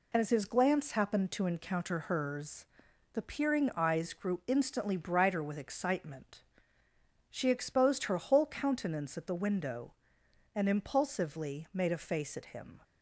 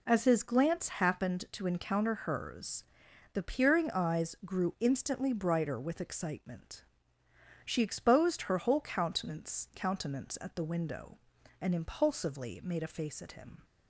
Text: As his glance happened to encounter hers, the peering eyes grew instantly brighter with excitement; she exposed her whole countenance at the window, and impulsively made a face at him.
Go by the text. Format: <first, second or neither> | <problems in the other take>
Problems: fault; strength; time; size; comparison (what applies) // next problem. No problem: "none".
first | says "countenance" twice; at 9.7 s